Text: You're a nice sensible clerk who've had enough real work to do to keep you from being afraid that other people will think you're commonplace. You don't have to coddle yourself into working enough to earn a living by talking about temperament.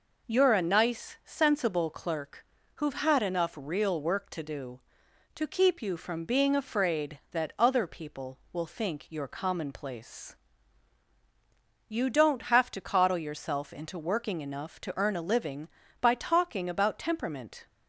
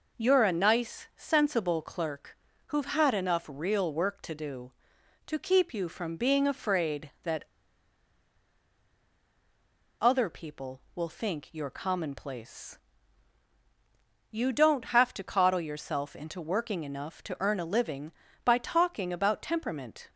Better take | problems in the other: first | pauses between "clerk" and "who've"; slight; at 2.3 s; 0.30 s long; slight in the first // pauses between "that" and "other"; strong; at 7.4 s; 2.5 s long

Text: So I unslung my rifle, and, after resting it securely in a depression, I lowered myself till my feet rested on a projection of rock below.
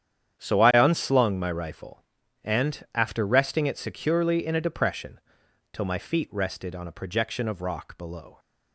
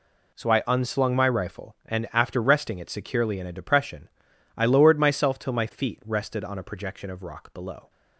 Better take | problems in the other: second | starts louder than the rest; strong; until 1.4 s; 9 dB // skips "I lowered myself"; at 5.4 s

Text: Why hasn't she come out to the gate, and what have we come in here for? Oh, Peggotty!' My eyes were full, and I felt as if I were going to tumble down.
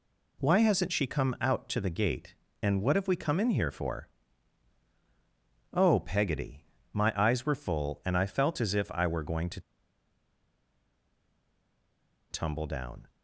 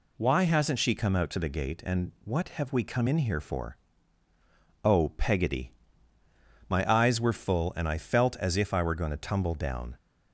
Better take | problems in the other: second | pauses between "to" and "tumble"; strong; at 9.5 s; 2.7 s long

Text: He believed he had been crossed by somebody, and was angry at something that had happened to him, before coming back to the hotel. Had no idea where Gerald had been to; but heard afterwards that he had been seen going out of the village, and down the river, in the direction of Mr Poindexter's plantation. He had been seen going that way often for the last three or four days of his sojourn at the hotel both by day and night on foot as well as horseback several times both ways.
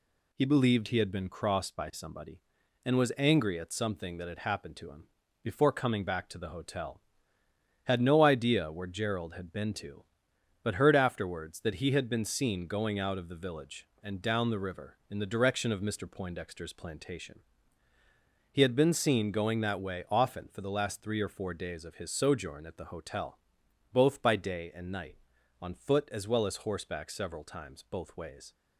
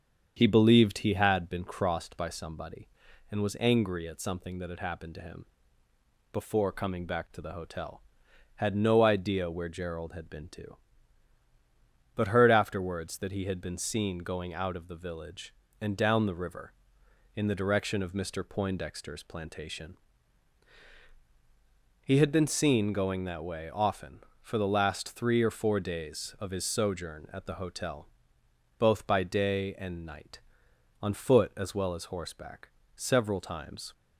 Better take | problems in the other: first | starts louder than the rest; strong; until 1.3 s; 7.5 dB // pauses between "hotel" and "both"; noticeable; at 28.0 s; 0.72 s long; noticeable in the first // pauses between "horseback" and "several"; slight; at 32.7 s; 0.26 s long // stops before "both ways"; at 33.9 s

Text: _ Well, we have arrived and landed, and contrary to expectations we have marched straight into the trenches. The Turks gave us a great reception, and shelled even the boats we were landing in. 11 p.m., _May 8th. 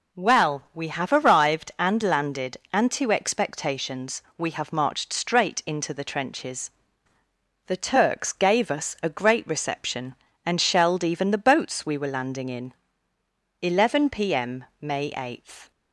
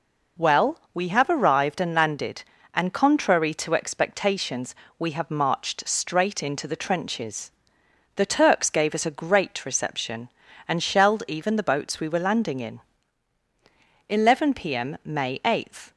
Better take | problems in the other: second | skips "contrary"; at 2.9 s // pauses between "expectations" and "we"; slight; at 4.2 s; 0.16 s long; slight in the second

